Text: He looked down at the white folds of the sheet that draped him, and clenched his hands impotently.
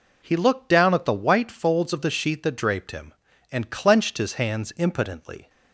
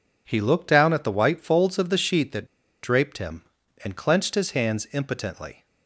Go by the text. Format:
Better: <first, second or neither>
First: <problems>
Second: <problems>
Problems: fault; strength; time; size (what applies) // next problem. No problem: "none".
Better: first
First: none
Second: pauses between "that" and "draped"; at 2.4 s; 0.37 s long